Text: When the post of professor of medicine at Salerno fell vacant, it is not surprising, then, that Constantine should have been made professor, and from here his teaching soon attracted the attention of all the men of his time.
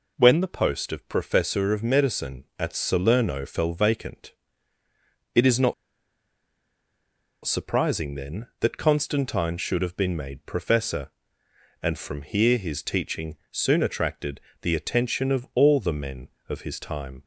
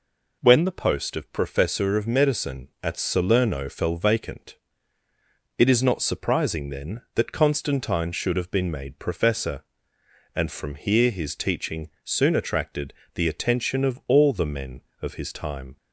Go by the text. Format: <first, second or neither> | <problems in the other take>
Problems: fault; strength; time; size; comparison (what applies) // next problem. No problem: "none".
second | pauses between "not" and "surprising"; strong; at 5.7 s; 1.7 s long // pauses between "teaching" and "soon"; slight; at 13.3 s; 0.16 s long; slight in the second // pauses between "attracted" and "the"; slight; at 14.3 s; 0.22 s long; slight in the second